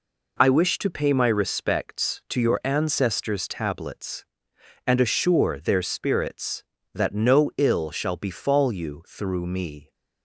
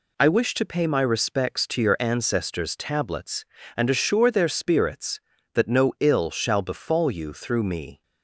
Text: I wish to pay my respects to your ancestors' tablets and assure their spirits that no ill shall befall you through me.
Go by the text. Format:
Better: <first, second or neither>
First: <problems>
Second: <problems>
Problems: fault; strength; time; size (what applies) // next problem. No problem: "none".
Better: neither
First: none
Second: none